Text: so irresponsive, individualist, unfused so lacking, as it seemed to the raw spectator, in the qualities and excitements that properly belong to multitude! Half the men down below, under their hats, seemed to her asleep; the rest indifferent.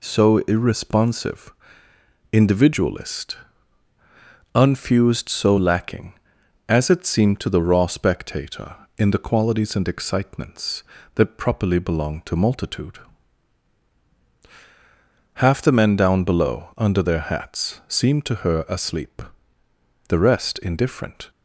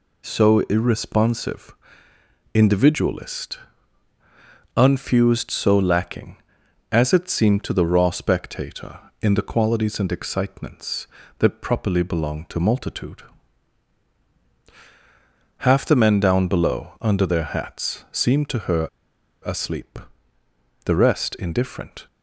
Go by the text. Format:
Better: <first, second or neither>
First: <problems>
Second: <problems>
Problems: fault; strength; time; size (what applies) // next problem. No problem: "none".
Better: first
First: none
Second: pauses between "her" and "asleep"; noticeable; at 18.8 s; 0.58 s long